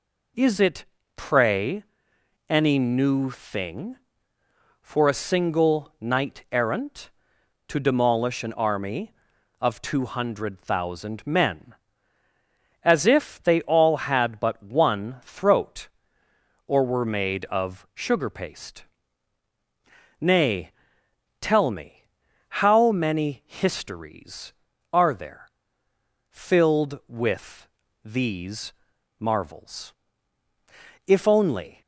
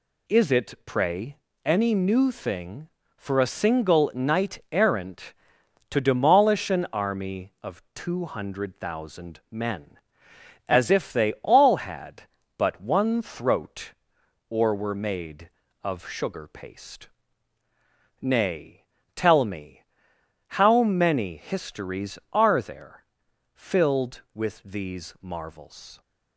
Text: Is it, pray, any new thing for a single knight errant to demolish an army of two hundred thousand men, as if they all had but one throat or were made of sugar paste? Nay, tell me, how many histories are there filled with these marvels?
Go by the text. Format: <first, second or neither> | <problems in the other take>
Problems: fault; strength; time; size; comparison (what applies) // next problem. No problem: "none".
second | pauses between "there" and "filled"; noticeable; at 25.4 s; 0.82 s long; noticeable in the second // pauses between "with" and "these"; slight; at 27.6 s; 0.36 s long // pauses between "these" and "marvels"; noticeable; at 28.7 s; 0.46 s long // goes on to say "If only"; noticeable; from 31.0 s on; 0.74 s long